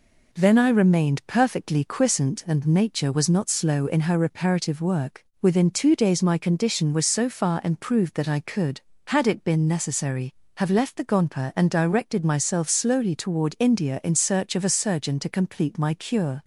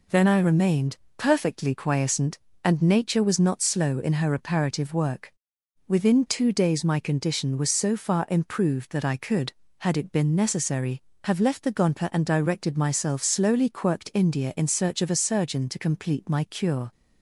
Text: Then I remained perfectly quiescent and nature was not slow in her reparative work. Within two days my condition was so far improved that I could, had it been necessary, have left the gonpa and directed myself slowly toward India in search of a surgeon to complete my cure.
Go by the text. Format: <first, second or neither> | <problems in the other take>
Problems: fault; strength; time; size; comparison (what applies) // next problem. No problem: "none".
first | pauses between "remained" and "perfectly"; slight; at 0.9 s; 0.20 s long // says "quirked" for "toward"; at 13.6 s